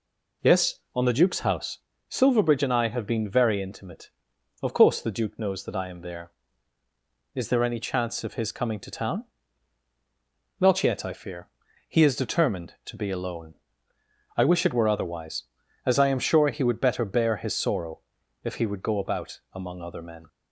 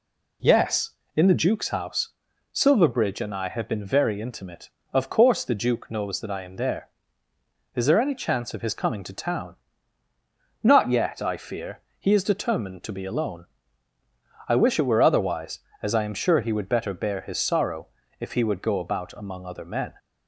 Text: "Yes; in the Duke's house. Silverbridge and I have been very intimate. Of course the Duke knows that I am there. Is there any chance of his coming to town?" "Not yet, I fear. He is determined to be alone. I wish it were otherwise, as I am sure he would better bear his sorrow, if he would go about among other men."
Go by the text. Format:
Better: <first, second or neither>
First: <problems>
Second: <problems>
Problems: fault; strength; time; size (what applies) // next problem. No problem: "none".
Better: second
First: says "on" for "in"; at 0.9 s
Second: none